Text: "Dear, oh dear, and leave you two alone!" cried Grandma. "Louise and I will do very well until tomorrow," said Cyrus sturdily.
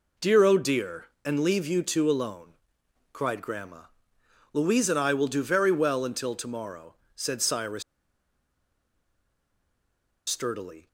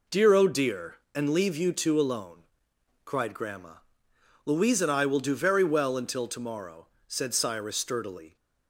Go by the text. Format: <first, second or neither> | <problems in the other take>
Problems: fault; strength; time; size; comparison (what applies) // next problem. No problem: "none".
second | pauses between "Cyrus" and "sturdily"; strong; at 7.8 s; 2.4 s long